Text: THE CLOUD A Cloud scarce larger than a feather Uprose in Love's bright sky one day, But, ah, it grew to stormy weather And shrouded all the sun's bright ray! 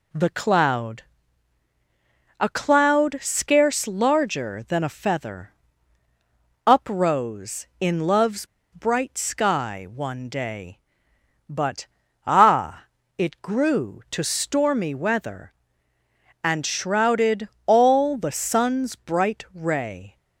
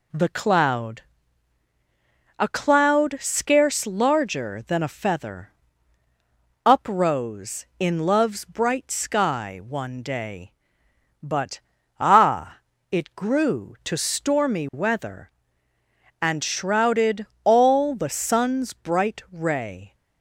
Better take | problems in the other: second | pauses between "CLOUD" and "A"; strong; at 1.0 s; 1.3 s long; strong in the second // pauses between "feather" and "Uprose"; at 5.5 s; 1.1 s long; also in the second // pauses between "Love's" and "bright"; slight; at 8.4 s; 0.26 s long // pauses between "shrouded" and "all"; slight; at 17.4 s; 0.18 s long; slight in the second

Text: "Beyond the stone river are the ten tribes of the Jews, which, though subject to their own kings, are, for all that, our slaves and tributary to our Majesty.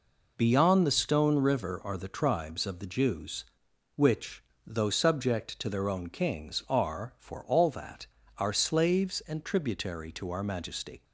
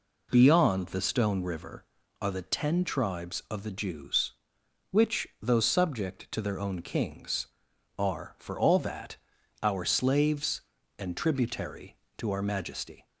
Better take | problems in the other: second | skips "ten"; at 2.0 s

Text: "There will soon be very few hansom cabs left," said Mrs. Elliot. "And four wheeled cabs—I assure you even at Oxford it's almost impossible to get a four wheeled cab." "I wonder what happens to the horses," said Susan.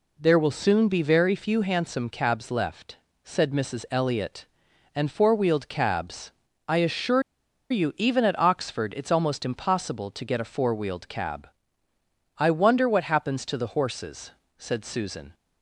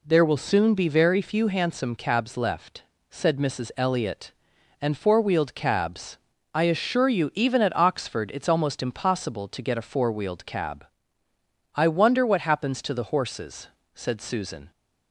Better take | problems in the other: second | pauses between "assure" and "you"; noticeable; at 7.2 s; 0.48 s long

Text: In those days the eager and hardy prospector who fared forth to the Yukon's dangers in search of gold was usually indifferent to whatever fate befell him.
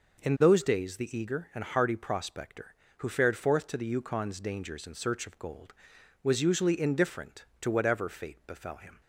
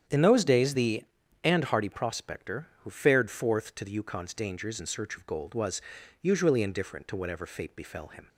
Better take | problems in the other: first | starts louder than the rest; strong; until 1.4 s; 9 dB // skips "eager"; at 1.2 s // pauses between "was" and "usually"; at 5.8 s; 0.40 s long

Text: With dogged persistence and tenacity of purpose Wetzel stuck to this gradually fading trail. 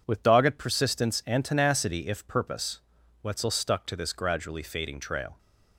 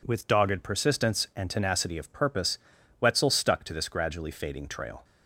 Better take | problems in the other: second | says "if" for "of"; at 2.0 s // pauses between "purpose" and "Wetzel"; at 2.7 s; 0.42 s long; also in the second

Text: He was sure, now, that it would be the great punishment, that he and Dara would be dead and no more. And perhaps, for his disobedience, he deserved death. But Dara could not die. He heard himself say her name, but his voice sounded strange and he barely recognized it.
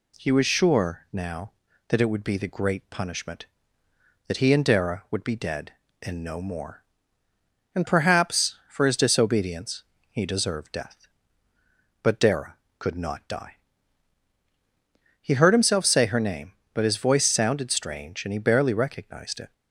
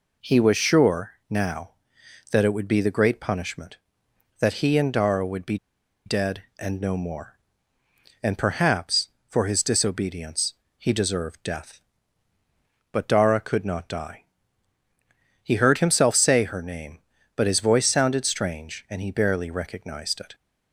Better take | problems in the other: first | pauses between "be" and "dead"; noticeable; at 5.5 s; 0.48 s long

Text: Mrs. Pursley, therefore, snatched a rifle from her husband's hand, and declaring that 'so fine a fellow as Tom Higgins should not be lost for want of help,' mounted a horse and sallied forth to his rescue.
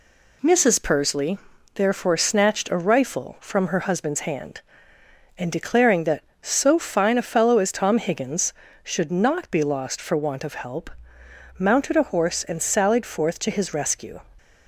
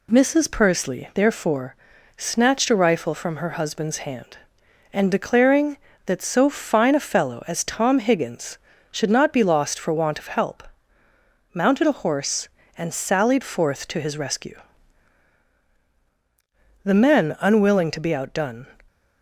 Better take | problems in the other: first | goes on to say "The men unwilling to be outdone"; strong; from 16.8 s on; 1.8 s long

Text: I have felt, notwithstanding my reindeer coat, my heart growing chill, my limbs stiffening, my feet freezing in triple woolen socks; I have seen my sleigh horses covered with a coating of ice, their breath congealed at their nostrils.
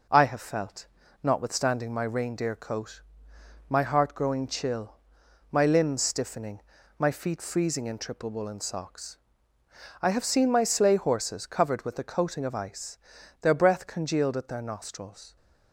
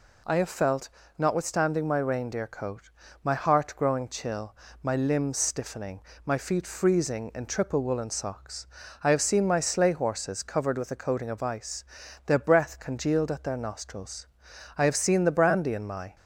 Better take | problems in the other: first | goes on to say "I have seen the brandy in my"; from 14.7 s on; 1.3 s long

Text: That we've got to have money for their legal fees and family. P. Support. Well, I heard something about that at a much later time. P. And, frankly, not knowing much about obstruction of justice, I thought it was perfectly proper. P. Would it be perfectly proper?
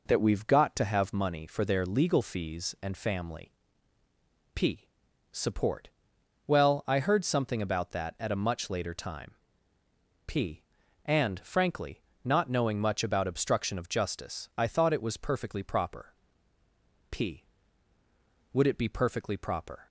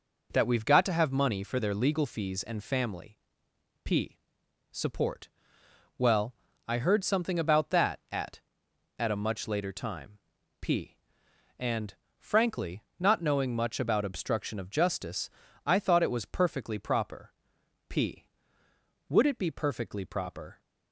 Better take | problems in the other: first | says "at" twice; at 8.9 s

